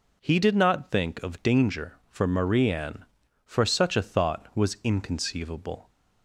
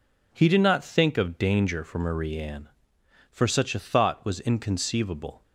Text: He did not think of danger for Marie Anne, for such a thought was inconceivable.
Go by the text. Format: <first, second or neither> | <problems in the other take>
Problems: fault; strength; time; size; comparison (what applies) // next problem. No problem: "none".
neither | none